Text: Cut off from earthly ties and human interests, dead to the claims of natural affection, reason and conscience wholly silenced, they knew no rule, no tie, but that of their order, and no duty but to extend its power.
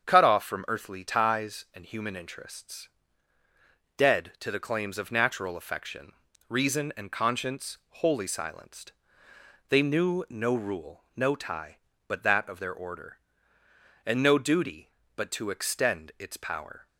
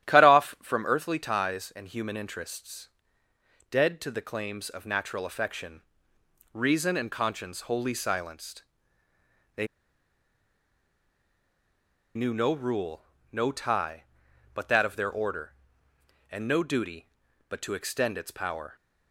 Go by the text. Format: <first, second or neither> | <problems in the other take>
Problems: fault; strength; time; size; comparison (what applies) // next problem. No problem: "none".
first | starts louder than the rest; strong; until 1.1 s; 12 dB; strong in the first // pauses between "they" and "knew"; strong; at 9.6 s; 2.5 s long